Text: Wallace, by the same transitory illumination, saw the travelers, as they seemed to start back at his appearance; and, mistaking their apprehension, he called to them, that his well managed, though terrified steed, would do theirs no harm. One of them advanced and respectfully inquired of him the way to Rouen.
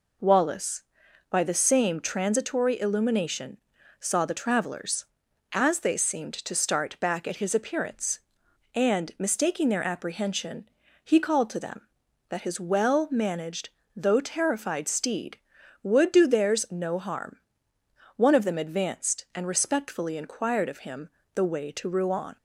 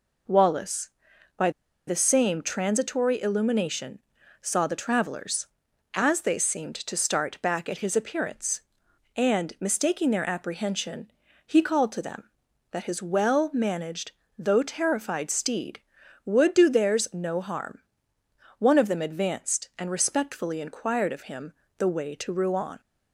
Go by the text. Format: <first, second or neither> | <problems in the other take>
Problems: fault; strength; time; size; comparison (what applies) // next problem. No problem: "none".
first | pauses between "by" and "the"; at 1.4 s; 0.37 s long // pauses between "him" and "the"; slight; at 21.5 s; 0.26 s long; slight in the first